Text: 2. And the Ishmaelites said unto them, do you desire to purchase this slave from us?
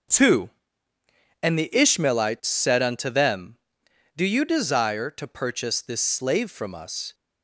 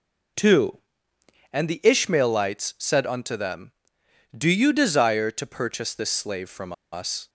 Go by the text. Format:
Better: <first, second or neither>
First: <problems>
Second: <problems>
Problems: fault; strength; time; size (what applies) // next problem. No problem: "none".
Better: first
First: none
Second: pauses between "from" and "us"; slight; at 6.7 s; 0.19 s long